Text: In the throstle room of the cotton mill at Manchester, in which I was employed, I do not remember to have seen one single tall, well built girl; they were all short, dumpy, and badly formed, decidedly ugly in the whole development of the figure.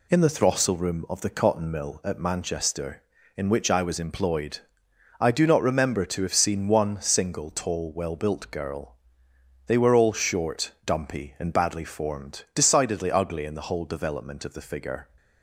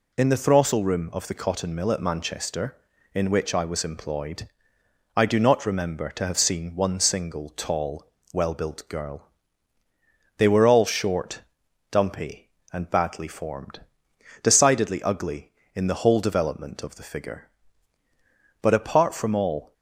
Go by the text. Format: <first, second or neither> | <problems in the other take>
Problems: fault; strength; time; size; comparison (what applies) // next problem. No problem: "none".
first | goes on to say "But apart from all"; noticeable; from 18.6 s on; 1.1 s long